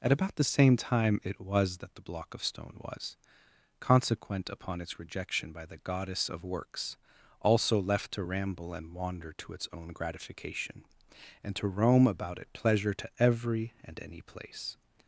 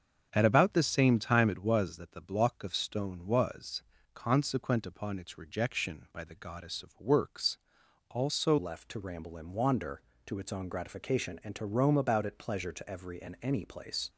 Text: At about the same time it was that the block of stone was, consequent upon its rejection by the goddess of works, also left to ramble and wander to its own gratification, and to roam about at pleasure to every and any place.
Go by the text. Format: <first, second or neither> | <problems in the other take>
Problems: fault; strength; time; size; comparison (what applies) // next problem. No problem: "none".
first | starts louder than the rest; until 1.3 s; 7 dB // changes voice at "left"; from 8.5 s on; 5.5 s long